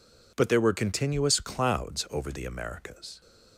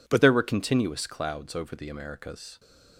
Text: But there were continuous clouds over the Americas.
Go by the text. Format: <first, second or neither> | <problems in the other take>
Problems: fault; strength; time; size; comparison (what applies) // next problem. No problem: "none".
first | changes voice at "there"; from 0.2 s on; 2.3 s long